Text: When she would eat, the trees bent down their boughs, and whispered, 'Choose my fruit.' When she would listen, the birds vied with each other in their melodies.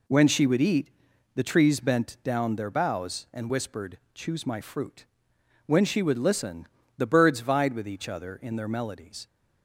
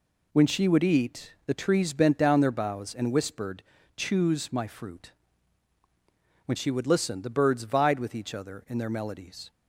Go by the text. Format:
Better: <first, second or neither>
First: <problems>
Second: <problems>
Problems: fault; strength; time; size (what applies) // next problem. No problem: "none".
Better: neither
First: none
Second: none